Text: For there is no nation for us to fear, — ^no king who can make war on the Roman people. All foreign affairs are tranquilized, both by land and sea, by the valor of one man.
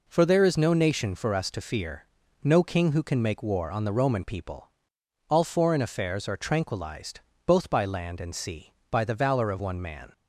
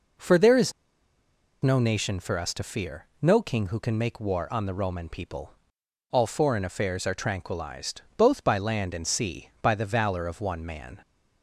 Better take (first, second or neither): first